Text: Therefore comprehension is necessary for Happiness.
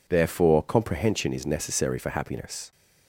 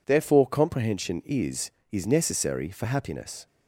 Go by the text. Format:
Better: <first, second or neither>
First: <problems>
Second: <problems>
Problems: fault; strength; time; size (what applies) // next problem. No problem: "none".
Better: first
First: none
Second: says "is" twice; at 1.9 s